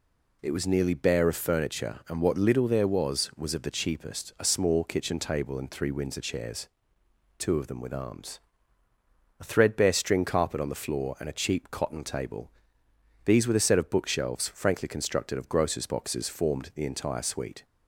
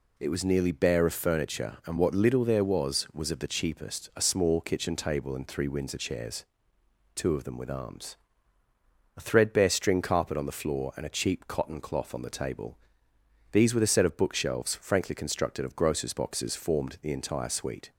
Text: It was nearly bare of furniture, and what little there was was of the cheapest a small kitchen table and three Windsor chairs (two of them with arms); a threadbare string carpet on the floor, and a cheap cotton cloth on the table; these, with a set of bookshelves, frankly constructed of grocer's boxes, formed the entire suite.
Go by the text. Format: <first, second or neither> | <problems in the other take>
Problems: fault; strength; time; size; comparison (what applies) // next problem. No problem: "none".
second | skips "cloth on the"; at 12.0 s